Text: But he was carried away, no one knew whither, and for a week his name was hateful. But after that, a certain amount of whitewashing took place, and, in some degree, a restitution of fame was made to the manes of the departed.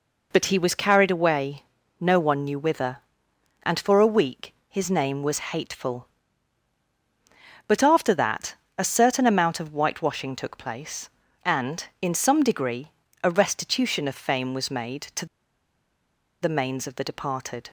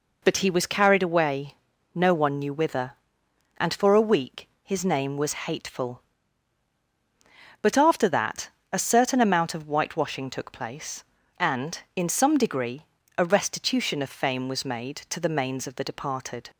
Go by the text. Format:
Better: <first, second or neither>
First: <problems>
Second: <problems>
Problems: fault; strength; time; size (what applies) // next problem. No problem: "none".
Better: second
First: pauses between "week" and "his"; slight; at 4.5 s; 0.16 s long // pauses between "to" and "the"; at 15.2 s; 1.1 s long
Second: pauses between "week" and "his"; slight; at 4.4 s; 0.16 s long